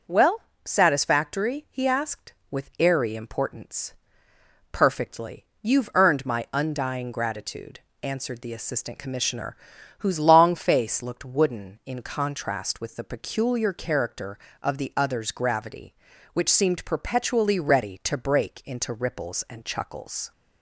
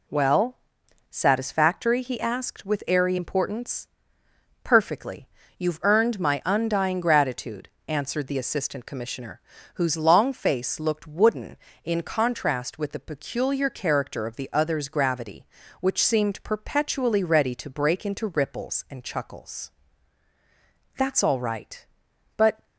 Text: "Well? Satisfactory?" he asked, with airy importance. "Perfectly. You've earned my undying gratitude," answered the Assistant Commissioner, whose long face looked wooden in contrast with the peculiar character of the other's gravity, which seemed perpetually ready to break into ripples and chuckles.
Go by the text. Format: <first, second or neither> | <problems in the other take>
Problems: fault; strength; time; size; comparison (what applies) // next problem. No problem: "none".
first | goes on to say "That's all right But"; strong; from 20.9 s on; 1.7 s long